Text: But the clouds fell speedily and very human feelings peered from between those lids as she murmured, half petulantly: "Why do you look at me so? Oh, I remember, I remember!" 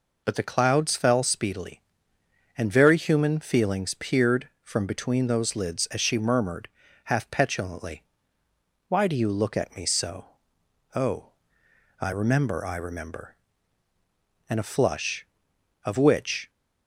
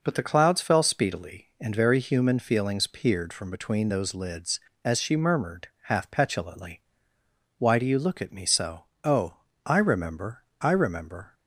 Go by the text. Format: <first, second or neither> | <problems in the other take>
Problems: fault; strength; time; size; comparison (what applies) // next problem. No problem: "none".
second | goes on to say "And a flush of which"; strong; from 14.4 s on; 2.0 s long